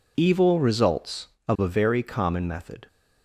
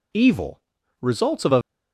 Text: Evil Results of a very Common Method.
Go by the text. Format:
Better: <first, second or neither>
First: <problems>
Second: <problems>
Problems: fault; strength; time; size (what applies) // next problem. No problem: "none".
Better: first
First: none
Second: pauses between "Evil" and "Results"; at 0.5 s; 0.42 s long // stops before "very Common Method"; at 1.6 s